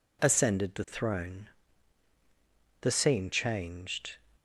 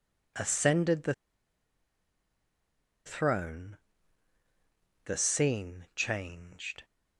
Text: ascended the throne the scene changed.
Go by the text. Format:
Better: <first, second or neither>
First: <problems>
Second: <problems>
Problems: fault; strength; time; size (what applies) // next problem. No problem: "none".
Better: first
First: pauses between "throne" and "the"; strong; at 1.4 s; 1.3 s long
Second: pauses between "the" and "throne"; strong; at 1.1 s; 1.9 s long // pauses between "throne" and "the"; strong; at 3.7 s; 1.2 s long